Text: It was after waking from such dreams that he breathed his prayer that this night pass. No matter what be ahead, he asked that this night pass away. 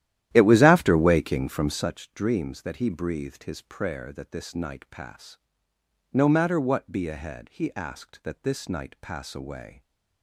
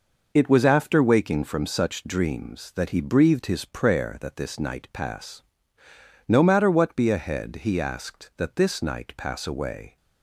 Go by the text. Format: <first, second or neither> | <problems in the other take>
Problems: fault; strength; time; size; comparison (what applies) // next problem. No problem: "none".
second | starts louder than the rest; strong; until 1.9 s; 12.5 dB